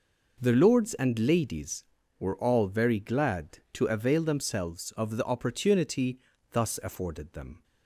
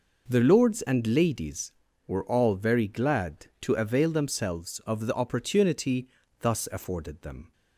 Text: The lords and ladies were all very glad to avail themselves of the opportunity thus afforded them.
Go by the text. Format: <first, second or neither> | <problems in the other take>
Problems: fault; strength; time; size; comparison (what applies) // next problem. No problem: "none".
neither | pauses between "opportunity" and "thus"; slight; the same in both